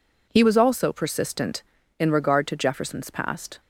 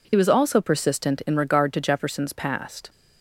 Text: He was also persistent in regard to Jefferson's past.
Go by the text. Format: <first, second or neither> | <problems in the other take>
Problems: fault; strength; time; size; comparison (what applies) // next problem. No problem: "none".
neither | none